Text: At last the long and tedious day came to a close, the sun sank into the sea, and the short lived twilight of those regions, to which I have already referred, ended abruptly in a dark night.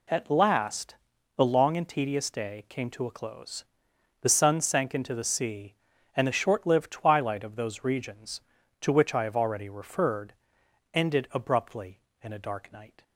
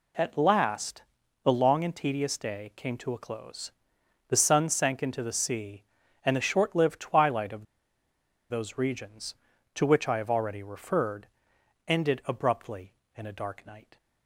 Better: first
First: pauses between "last" and "the"; at 0.9 s; 0.42 s long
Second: pauses between "last" and "the"; at 1.0 s; 0.42 s long // pauses between "of" and "those"; noticeable; at 7.6 s; 0.85 s long

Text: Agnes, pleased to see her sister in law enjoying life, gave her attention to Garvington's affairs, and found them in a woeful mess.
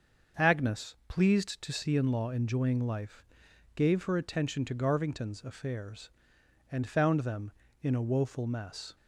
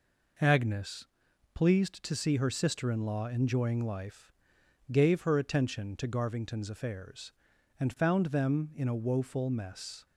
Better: second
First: starts louder than the rest; until 1.5 s; 6.5 dB // skips "her sister"; at 1.9 s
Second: none

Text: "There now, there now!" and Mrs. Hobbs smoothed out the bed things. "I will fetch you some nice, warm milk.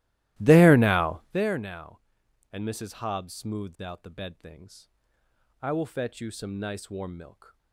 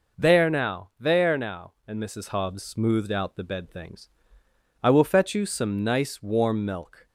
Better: second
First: starts louder than the rest; strong; until 1.5 s; 16 dB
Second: none

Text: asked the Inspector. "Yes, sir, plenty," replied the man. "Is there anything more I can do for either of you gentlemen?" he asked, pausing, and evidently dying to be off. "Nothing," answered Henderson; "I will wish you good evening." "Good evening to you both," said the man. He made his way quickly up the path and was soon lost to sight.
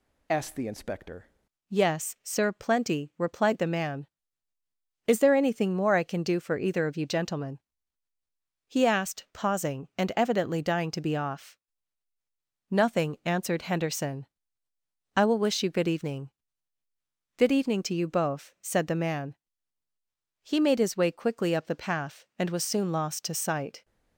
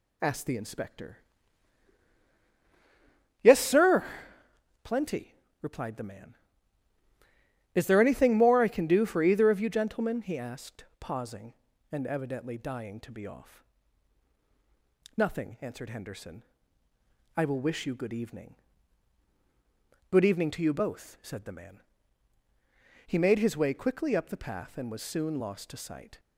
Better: second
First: changes voice at "Yes"; from 1.6 s on; 22.2 s long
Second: none

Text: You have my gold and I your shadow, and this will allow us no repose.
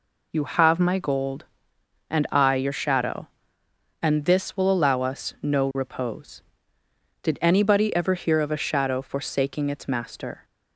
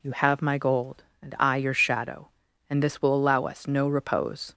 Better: second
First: goes on to say "Did anybody ever hear of a shadow forsaking its master"; strong; from 7.2 s on; 3.2 s long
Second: none

